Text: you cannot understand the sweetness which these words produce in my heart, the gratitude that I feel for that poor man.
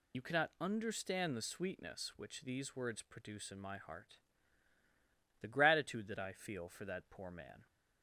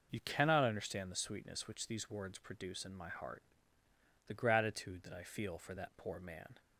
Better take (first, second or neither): second